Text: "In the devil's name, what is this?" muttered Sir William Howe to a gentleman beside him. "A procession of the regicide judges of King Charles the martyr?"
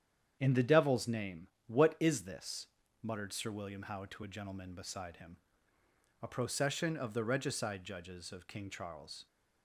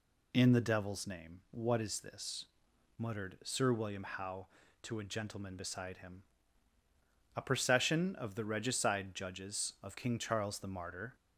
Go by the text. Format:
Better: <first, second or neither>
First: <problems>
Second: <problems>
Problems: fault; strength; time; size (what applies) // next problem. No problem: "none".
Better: second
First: starts louder than the rest; strong; until 1.4 s; 9 dB // stops before "the martyr"; at 9.2 s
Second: none